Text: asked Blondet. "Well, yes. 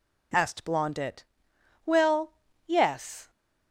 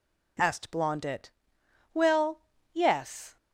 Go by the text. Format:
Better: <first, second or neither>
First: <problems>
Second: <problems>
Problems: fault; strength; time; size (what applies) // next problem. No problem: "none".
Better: neither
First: none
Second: none